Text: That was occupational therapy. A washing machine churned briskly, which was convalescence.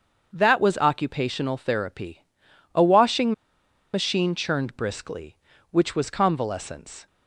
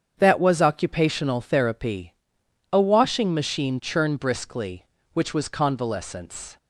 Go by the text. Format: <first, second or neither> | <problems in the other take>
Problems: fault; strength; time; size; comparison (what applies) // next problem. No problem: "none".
second | starts louder than the rest; until 1.3 s; 6.5 dB; strong in the second // pauses between "washing" and "machine"; noticeable; at 3.3 s; 0.60 s long